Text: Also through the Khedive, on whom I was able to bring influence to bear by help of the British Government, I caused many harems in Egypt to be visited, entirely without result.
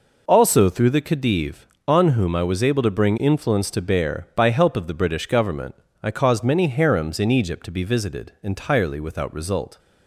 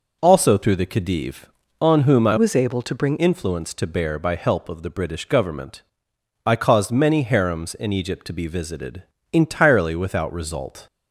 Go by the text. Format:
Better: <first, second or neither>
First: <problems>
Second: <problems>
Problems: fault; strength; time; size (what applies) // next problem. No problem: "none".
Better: first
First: none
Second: changes voice from "was" to "bring"; from 2.3 to 3.1 s; 0.8 s long